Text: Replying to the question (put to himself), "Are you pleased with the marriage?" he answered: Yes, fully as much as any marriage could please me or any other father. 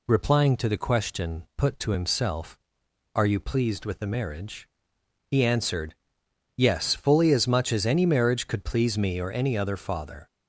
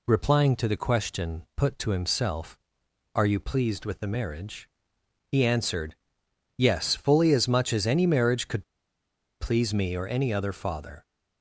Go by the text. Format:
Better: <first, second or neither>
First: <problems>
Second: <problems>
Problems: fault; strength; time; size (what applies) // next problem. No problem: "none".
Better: first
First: none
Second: pauses between "could" and "please"; noticeable; at 8.6 s; 0.75 s long